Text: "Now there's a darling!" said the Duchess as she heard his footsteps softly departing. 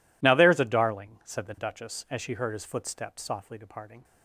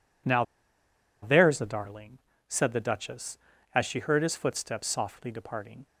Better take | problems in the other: first | pauses between "Now" and "there's"; noticeable; at 0.4 s; 0.79 s long

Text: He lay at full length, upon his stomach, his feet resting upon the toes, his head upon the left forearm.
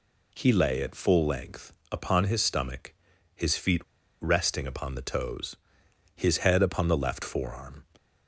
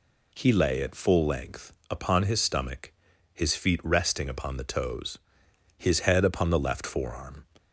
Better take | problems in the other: second | pauses between "feet" and "resting"; at 3.8 s; 0.38 s long

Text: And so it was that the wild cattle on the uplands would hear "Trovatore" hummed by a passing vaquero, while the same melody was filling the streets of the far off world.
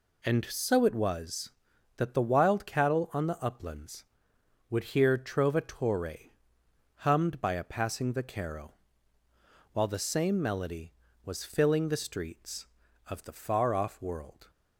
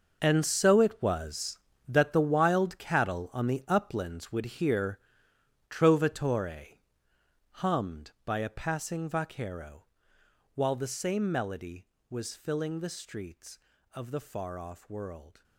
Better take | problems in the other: first | gets quieter; strong; throughout; 14.5 dB // pauses between "hear" and "Trovatore"; noticeable; at 4.9 s; 0.72 s long // pauses between "Trovatore" and "hummed"; noticeable; at 6.7 s; 0.72 s long; noticeable in the first

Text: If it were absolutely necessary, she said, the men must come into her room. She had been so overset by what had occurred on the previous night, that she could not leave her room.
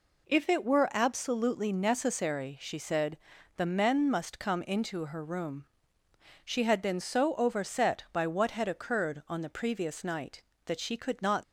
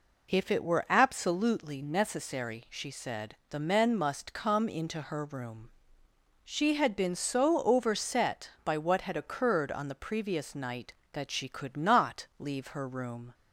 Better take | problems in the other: second | stops before "leave her room"; at 11.4 s

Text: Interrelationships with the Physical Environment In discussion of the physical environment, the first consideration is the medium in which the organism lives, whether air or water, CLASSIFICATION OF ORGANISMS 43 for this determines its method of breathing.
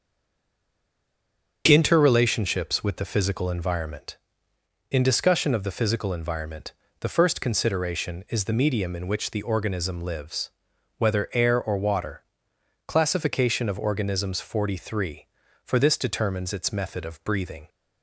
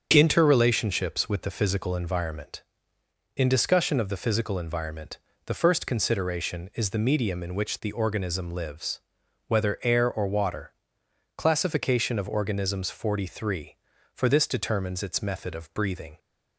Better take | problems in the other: second | stays silent before the first word; noticeable; until 1.6 s; 1.6 s long // starts louder than the rest; strong; until 2.6 s; 7 dB; strong in the second

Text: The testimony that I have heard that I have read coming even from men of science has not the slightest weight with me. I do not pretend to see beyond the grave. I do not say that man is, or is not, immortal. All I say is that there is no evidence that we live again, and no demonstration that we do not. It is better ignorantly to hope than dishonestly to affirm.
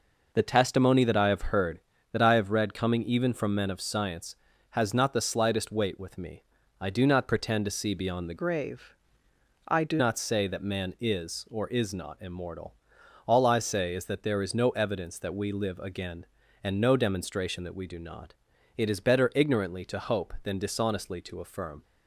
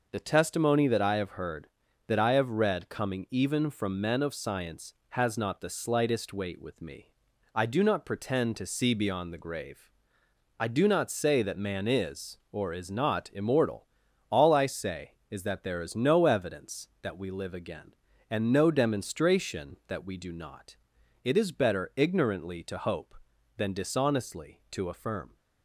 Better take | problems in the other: second | changes voice from "grave" to "do"; from 8.3 to 10.0 s; 1.7 s long

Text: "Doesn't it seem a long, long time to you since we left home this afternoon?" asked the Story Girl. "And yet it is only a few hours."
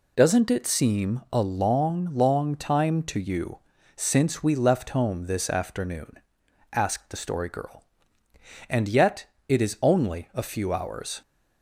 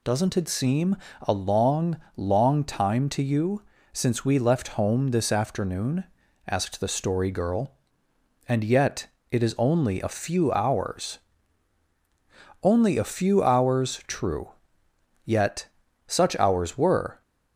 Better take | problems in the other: first | pauses between "seem" and "a"; slight; at 0.9 s; 0.24 s long // pauses between "you" and "since"; slight; at 3.6 s; 0.30 s long; slight in the first // pauses between "yet" and "it"; slight; at 9.0 s; 0.24 s long; slight in the first // goes on to say "Only a few hours true yet such hours were"; strong; from 12.6 s on; 4.5 s long

